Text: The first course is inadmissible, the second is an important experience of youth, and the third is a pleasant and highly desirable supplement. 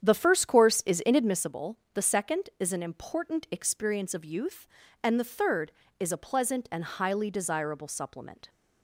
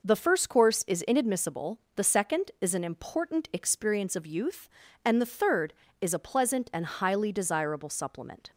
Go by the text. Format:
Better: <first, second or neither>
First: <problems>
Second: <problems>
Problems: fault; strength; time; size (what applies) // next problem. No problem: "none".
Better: second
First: starts louder than the rest; strong; until 1.6 s; 8.5 dB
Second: none